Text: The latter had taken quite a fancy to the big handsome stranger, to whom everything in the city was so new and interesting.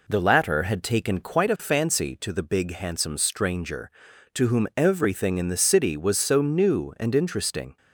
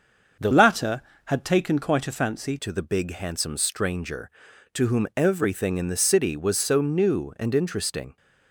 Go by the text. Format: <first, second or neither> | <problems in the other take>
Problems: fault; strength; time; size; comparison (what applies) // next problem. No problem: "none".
first | starts louder than the rest; until 1.6 s; 6.5 dB // changes voice from "latter" to "fancy"; from 0.5 to 2.5 s; 2.0 s long